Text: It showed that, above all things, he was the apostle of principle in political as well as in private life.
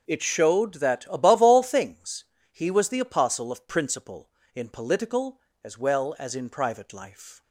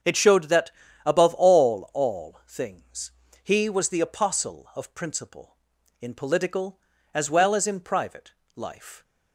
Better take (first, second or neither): first